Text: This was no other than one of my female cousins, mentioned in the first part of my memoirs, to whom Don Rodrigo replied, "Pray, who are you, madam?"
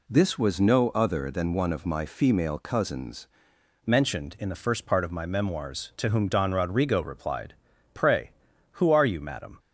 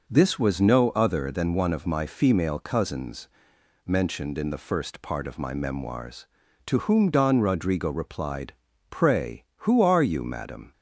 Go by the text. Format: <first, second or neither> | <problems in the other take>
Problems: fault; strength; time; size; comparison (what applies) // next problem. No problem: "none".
second | changes voice at "mentioned"; from 3.8 s on; 5.7 s long